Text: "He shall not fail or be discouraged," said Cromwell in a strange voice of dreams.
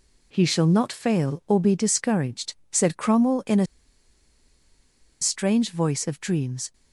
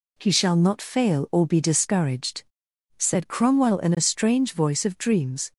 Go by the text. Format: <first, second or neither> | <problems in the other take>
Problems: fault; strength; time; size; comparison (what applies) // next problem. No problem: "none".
second | pauses between "a" and "strange"; strong; at 3.6 s; 1.5 s long